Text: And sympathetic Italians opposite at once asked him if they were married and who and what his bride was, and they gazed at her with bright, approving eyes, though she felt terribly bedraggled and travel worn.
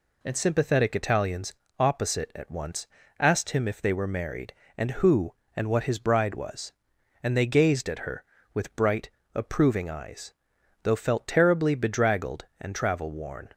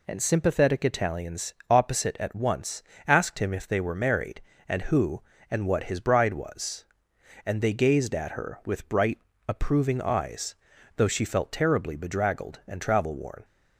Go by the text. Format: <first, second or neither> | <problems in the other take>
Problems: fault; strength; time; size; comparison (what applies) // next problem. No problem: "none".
second | pauses between "Italians" and "opposite"; slight; at 1.5 s; 0.24 s long // pauses between "once" and "asked"; slight; at 2.8 s; 0.32 s long; slight in the second // skips "she"; at 10.9 s